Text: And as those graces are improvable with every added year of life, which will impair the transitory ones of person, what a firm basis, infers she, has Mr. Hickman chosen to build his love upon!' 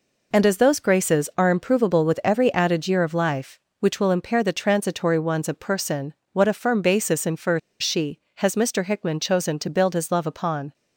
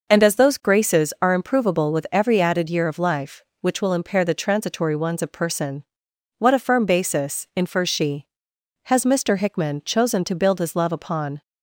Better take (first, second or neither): second